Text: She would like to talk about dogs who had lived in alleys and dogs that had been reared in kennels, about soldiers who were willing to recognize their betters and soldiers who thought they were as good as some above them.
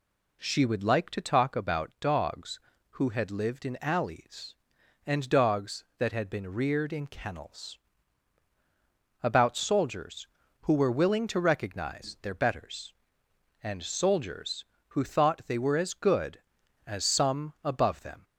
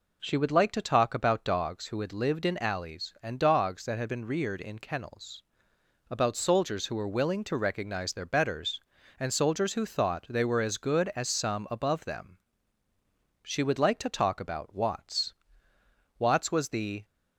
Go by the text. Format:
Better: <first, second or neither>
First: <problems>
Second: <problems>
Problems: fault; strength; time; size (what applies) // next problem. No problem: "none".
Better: first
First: none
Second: goes on to say "She would like to talk about Watts Watts was the"; strong; from 13.4 s on; 3.6 s long